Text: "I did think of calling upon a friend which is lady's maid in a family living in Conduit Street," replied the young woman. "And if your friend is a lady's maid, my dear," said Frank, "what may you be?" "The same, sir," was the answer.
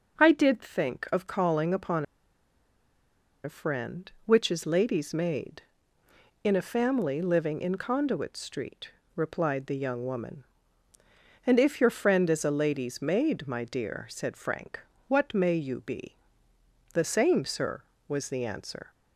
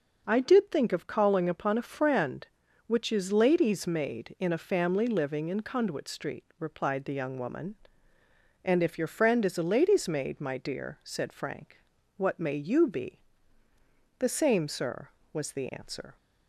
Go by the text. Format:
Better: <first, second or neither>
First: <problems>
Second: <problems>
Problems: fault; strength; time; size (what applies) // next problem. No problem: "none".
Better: second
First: pauses between "upon" and "a"; strong; at 2.0 s; 1.3 s long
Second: none